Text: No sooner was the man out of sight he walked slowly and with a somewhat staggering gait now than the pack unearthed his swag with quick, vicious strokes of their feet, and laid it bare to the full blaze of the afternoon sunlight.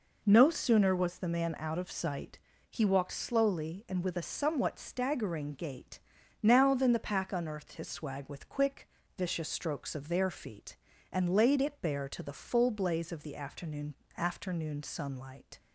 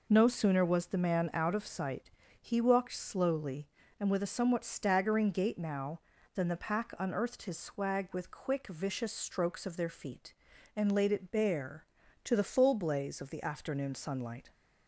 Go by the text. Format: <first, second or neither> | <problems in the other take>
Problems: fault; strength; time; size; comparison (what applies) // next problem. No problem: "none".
second | pauses between "sight" and "he"; slight; at 2.3 s; 0.32 s long; slight in the second // pauses between "gait" and "now"; at 5.9 s; 0.44 s long // says "afternoon" twice; at 14.1 s